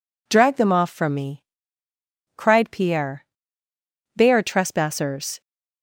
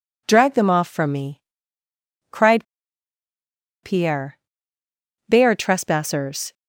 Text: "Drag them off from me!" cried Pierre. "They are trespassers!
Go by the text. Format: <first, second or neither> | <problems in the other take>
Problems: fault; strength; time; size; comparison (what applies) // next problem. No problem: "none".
first | pauses between "cried" and "Pierre"; at 2.6 s; 1.1 s long